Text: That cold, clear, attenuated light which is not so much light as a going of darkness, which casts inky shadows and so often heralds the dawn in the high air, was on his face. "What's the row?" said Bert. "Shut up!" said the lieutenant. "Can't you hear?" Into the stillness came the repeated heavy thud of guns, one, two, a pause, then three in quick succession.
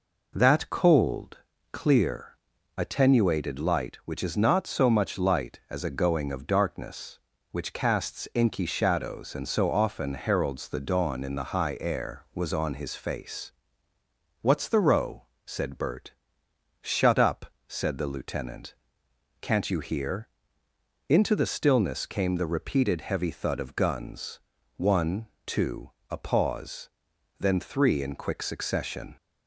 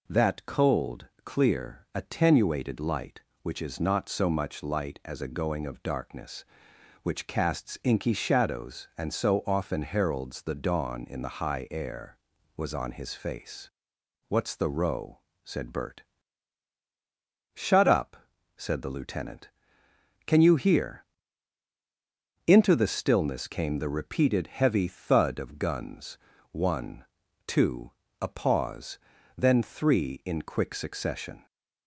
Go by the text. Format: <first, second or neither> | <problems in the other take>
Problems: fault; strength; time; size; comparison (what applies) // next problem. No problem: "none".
first | says "Can" for "Can't"; at 20.2 s